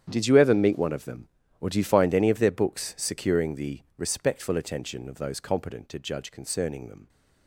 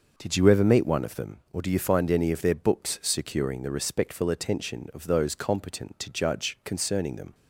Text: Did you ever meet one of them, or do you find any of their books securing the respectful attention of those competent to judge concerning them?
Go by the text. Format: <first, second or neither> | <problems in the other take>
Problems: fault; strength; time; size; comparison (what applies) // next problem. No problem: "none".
second | gets quieter; strong; throughout; 15 dB // pauses between "the" and "respectful"; slight; at 3.8 s; 0.16 s long